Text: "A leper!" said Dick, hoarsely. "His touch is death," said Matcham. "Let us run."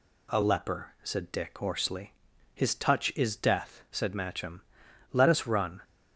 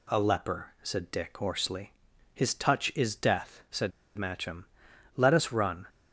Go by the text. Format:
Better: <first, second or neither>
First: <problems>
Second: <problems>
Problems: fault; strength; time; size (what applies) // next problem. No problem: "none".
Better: first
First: none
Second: pauses between "said" and "Matcham"; slight; at 3.9 s; 0.25 s long